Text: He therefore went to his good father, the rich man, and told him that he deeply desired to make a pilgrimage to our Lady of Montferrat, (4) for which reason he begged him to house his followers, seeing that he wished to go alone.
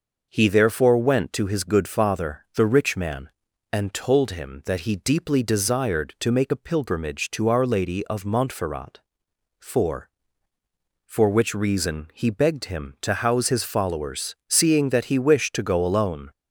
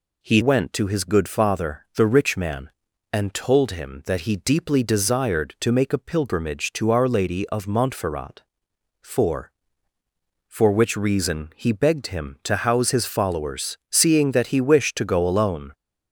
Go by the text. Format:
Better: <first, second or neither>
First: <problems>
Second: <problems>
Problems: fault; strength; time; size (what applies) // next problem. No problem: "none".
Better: first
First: none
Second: skips "therefore"; at 0.4 s